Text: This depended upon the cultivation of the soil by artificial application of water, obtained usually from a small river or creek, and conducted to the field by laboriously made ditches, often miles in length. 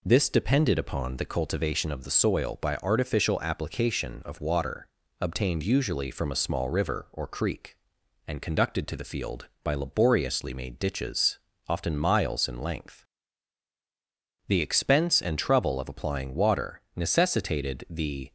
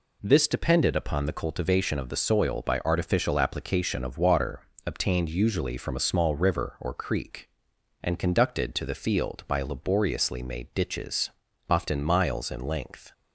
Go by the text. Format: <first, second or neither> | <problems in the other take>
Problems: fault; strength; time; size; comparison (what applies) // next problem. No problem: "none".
second | goes on to say "The expense and trouble of applying water necessitated the"; strong; from 14.4 s on; 3.8 s long